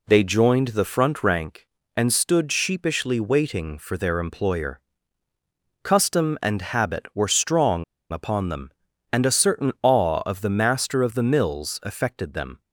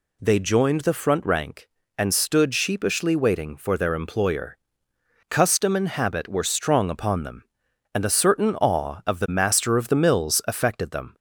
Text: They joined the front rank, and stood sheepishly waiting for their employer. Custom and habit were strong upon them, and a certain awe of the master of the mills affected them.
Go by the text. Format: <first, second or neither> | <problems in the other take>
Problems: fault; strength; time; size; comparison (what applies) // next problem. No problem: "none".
second | pauses between "strong" and "upon"; slight; at 7.8 s; 0.28 s long